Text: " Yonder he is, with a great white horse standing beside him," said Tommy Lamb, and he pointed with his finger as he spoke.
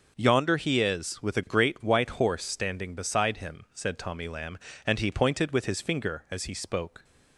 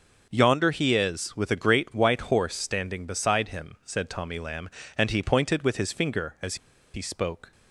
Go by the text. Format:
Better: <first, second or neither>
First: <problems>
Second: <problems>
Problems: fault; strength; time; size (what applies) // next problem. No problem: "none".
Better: first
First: none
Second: pauses between "as" and "he"; at 6.5 s; 0.37 s long